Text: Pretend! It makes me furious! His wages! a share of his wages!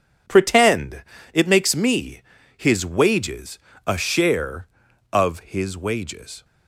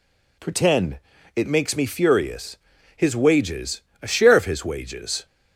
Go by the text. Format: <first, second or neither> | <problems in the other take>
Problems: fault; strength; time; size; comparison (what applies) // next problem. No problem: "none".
second | skips "furious"; at 2.3 s